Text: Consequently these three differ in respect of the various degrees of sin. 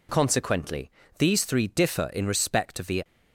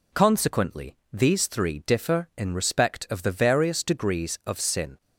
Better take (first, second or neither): second